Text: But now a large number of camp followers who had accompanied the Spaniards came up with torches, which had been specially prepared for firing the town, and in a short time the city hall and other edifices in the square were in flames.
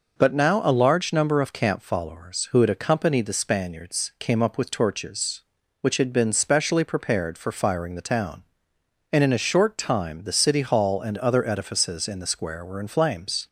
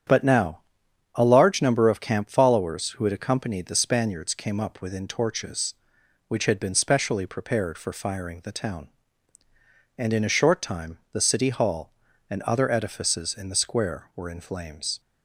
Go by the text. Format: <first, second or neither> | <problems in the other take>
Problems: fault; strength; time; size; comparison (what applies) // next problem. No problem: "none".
first | starts louder than the rest; strong; until 1.6 s; 9 dB // pauses between "now" and "a"; noticeable; at 0.5 s; 0.54 s long // says "within" for "with"; at 4.7 s